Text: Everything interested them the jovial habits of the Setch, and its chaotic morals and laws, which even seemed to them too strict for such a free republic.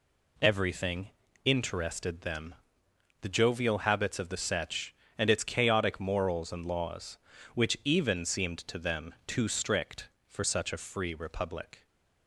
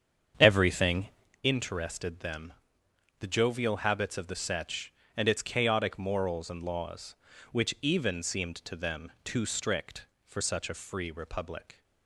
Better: first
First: pauses between "Everything" and "interested"; slight; at 1.0 s; 0.36 s long // pauses between "them" and "the"; noticeable; at 2.5 s; 0.68 s long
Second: starts louder than the rest; strong; until 1.4 s; 8 dB // pauses between "Everything" and "interested"; slight; at 1.0 s; 0.36 s long // pauses between "them" and "the"; noticeable; at 2.5 s; 0.68 s long

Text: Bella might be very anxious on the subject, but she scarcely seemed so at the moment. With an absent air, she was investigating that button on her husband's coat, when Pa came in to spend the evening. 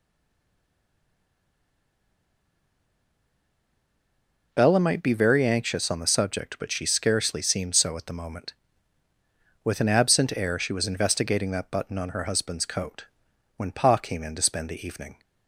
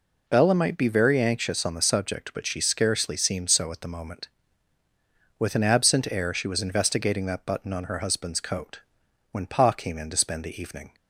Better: second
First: stays silent before the first word; strong; until 4.5 s; 4.5 s long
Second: none

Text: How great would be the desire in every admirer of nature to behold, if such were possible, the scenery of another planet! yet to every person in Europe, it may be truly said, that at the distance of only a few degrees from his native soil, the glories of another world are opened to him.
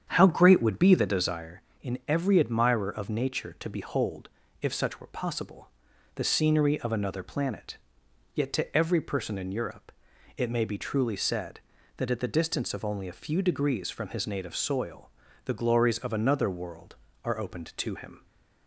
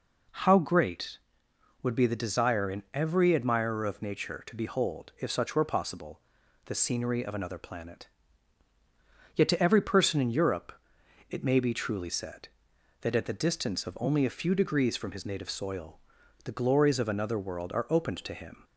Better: second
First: starts louder than the rest; strong; until 1.4 s; 8.5 dB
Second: none

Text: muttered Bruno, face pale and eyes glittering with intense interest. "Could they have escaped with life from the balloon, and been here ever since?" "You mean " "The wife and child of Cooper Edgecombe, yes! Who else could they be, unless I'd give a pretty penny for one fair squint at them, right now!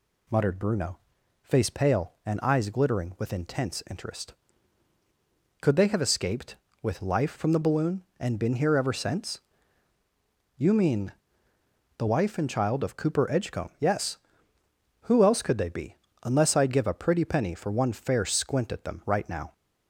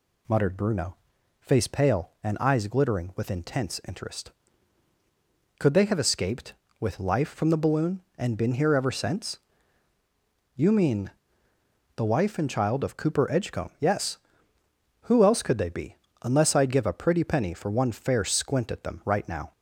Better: neither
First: none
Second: none

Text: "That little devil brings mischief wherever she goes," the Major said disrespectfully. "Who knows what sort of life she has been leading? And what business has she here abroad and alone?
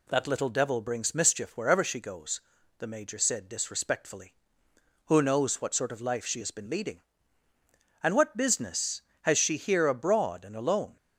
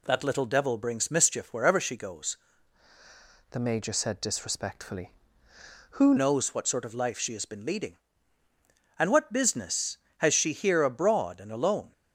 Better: first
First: none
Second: changes voice from "the" to "Who"; from 3.5 to 6.1 s; 2.6 s long

